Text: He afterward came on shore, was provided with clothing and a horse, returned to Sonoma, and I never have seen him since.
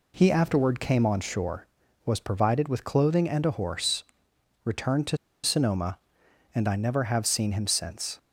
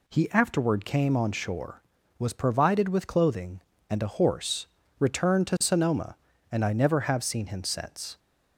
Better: second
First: pauses between "to" and "Sonoma"; slight; at 5.1 s; 0.26 s long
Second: none

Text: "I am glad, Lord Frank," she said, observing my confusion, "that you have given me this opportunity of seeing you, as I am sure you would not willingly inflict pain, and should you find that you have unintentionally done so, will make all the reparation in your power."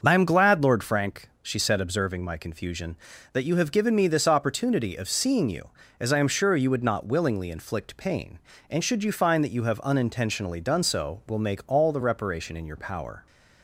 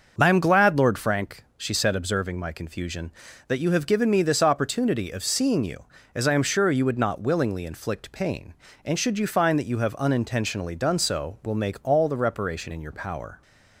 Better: neither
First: starts louder than the rest; until 1.0 s; 6.5 dB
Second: starts louder than the rest; until 1.1 s; 6.5 dB

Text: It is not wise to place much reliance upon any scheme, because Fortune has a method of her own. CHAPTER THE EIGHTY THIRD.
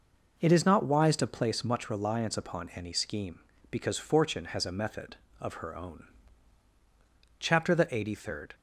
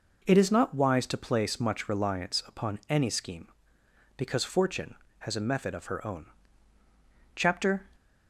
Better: first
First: none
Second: stops before "THE EIGHTY THIRD"; at 7.9 s

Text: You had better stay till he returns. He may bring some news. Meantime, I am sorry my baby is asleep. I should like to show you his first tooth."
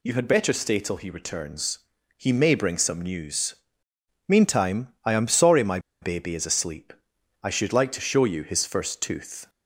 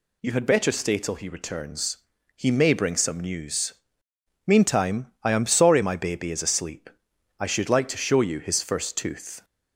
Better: second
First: pauses between "my" and "baby"; slight; at 5.7 s; 0.22 s long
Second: none

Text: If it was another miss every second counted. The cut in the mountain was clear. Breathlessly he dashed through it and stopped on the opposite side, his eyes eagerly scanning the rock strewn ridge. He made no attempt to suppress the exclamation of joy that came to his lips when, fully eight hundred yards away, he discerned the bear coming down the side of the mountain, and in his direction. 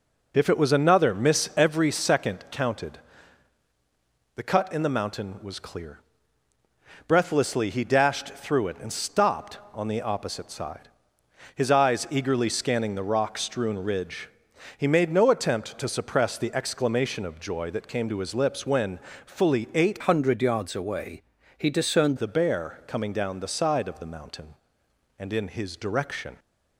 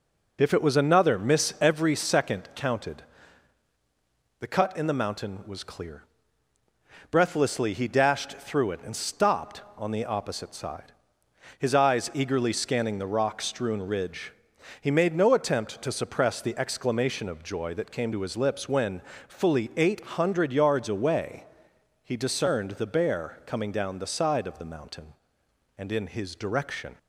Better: second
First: changes voice from "hundred" to "discerned"; from 20.0 to 22.1 s; 2.1 s long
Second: none

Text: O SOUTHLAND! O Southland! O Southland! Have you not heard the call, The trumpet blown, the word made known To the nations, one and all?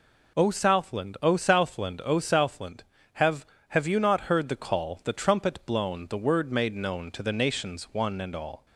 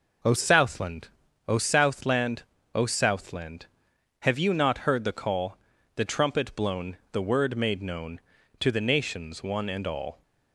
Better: second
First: says "Have" twice; at 3.6 s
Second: none

